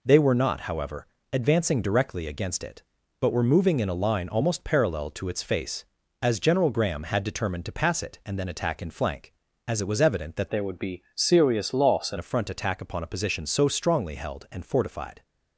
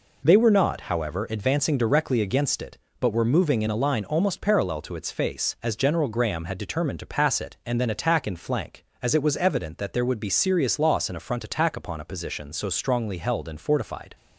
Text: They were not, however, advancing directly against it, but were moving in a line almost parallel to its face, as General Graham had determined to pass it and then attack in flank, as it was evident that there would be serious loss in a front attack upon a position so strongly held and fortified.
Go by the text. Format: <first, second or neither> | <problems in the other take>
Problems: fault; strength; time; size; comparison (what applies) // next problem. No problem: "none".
second | changes voice from "there" to "in"; from 10.4 to 12.1 s; 1.7 s long